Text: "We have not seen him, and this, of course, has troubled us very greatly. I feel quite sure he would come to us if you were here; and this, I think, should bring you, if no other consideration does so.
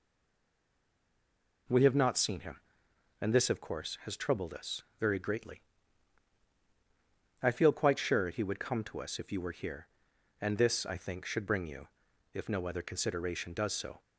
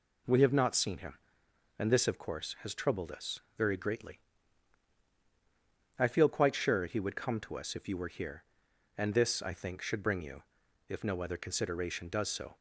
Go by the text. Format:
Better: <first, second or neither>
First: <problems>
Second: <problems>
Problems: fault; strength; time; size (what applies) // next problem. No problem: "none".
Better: second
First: stays silent before the first word; noticeable; until 1.6 s; 1.6 s long // pauses between "us" and "very"; slight; at 4.8 s; 0.18 s long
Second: pauses between "us" and "very"; slight; at 3.4 s; 0.18 s long